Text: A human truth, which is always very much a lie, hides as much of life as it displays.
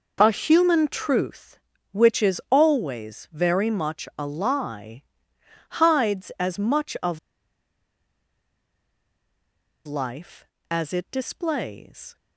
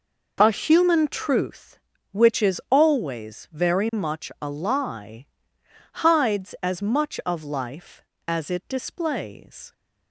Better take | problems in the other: second | pauses between "of" and "life"; strong; at 7.1 s; 2.6 s long

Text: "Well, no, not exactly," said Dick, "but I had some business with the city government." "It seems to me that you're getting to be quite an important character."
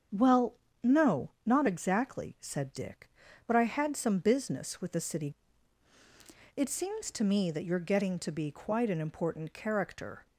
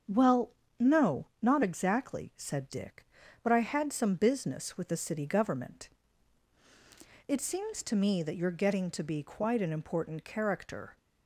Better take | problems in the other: second | starts louder than the rest; until 1.5 s; 7 dB; also in the second // skips "government"; at 5.9 s

